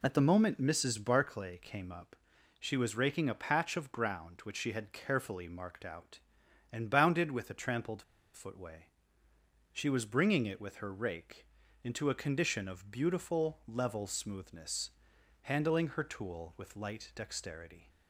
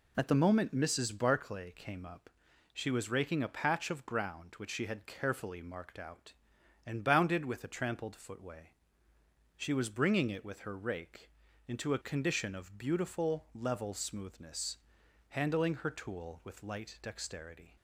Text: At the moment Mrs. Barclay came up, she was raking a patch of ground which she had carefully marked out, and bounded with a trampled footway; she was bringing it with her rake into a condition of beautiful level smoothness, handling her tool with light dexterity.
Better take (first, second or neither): second